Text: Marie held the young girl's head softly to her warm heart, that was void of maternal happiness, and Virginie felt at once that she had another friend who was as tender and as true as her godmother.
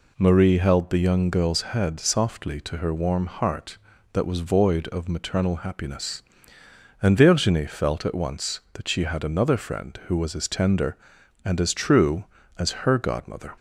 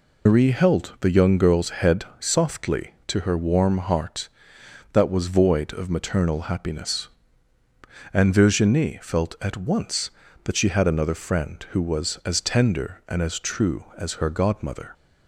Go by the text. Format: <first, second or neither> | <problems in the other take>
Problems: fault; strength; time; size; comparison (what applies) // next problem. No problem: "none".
first | loses the start of "Marie"; at 0.2 s; 100 ms